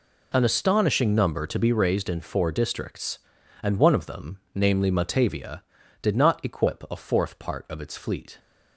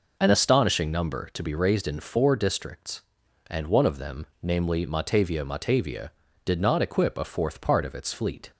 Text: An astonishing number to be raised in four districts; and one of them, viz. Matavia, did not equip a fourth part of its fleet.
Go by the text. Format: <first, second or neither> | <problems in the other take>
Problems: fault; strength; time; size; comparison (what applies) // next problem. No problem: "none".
first | says "Matavia" twice; at 5.4 s